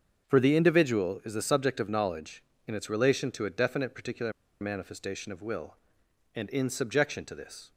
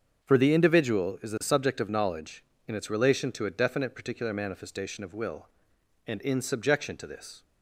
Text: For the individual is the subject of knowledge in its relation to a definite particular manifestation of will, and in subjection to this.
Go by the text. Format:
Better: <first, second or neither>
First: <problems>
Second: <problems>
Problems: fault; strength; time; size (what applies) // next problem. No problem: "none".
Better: second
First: starts louder than the rest; until 1.2 s; 7 dB // pauses between "particular" and "manifestation"; slight; at 4.3 s; 0.28 s long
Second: starts louder than the rest; until 1.2 s; 6.5 dB